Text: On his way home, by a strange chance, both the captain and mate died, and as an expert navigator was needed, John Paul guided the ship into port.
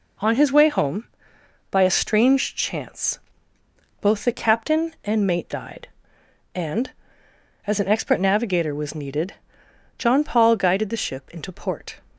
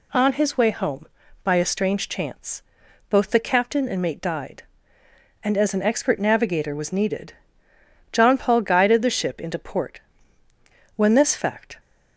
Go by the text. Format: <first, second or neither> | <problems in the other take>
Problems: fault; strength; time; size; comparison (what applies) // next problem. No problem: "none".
first | goes on to say "When this fact"; noticeable; from 10.9 s on; 0.84 s long